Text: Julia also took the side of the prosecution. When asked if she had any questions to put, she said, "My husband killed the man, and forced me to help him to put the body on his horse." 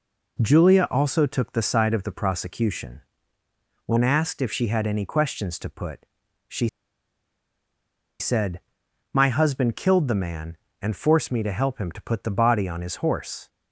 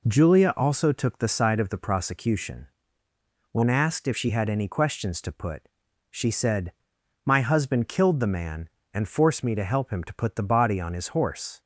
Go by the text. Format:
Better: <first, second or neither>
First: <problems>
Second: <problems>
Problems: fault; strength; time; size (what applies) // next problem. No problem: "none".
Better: second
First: pauses between "she" and "said"; strong; at 6.6 s; 1.5 s long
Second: none